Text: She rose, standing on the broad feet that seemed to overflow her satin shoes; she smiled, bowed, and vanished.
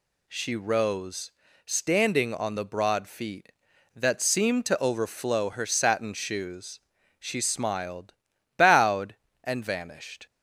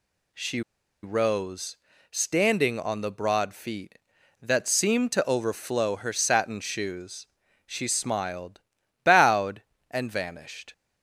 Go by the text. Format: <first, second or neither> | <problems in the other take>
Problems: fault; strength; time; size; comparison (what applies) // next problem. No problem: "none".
first | pauses between "She" and "rose"; at 0.6 s; 0.42 s long